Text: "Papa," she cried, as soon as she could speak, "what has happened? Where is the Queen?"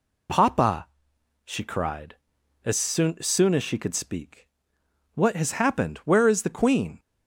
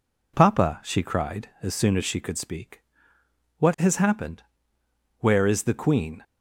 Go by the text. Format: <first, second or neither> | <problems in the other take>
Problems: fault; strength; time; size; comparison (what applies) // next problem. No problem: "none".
second | says "soon" twice; at 3.2 s